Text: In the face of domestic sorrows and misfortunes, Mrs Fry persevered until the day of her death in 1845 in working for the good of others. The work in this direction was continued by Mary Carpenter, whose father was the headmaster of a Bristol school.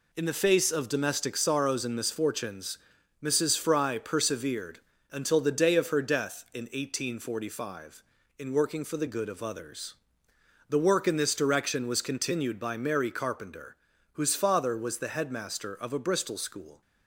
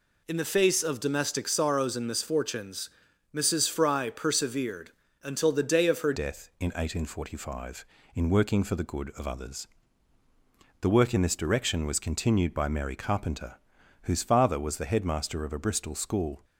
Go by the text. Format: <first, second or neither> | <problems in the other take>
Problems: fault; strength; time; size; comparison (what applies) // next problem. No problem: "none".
first | pauses between "persevered" and "until"; slight; at 4.9 s; 0.30 s long; slight in the first // changes voice at "death"; from 6.1 s on; 10.3 s long